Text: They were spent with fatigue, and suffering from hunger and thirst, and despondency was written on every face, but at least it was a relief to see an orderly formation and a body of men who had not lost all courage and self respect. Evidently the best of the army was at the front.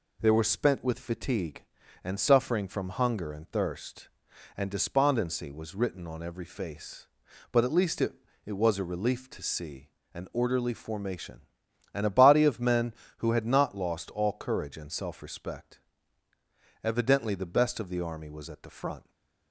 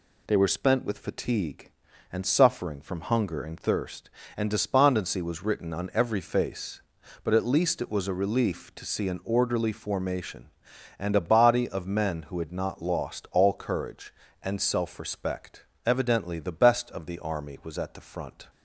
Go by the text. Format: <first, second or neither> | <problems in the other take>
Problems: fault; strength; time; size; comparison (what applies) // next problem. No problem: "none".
second | says "it" twice; at 8.4 s // pauses between "see" and "an"; slight; at 9.8 s; 0.24 s long